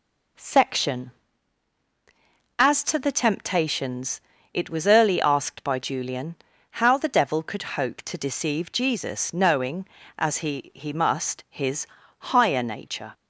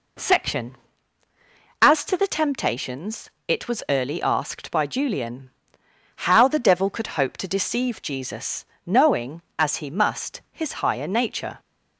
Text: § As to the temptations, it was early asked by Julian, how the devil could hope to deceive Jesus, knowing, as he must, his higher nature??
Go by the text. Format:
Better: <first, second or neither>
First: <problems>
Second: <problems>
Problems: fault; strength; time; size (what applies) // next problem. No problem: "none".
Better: second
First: says "he" twice; at 10.7 s // pauses between "his" and "higher"; slight; at 11.8 s; 0.32 s long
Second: none